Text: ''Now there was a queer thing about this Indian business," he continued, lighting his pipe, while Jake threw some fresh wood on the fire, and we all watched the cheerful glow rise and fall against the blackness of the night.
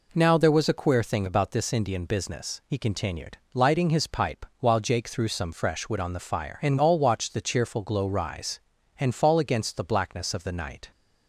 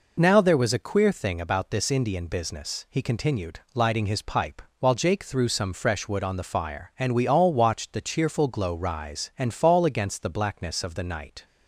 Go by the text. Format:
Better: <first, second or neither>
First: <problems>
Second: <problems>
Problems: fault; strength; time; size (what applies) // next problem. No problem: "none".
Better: second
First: skips "we"; at 6.7 s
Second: none